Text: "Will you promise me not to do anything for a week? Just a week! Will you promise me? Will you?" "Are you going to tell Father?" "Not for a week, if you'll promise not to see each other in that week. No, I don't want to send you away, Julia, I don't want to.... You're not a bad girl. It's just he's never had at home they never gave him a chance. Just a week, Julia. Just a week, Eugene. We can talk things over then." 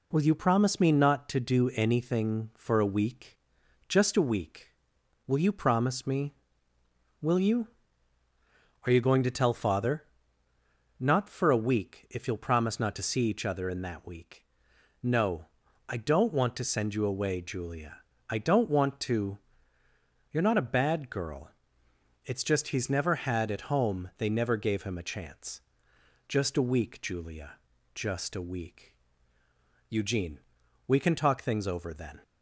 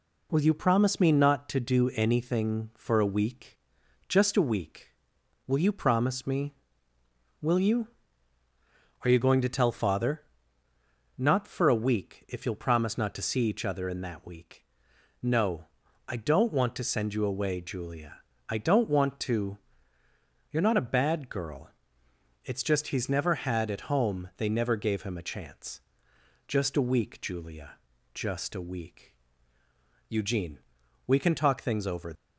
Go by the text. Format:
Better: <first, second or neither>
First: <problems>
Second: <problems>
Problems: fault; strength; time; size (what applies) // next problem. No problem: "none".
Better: first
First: none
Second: stops before "then"; at 32.1 s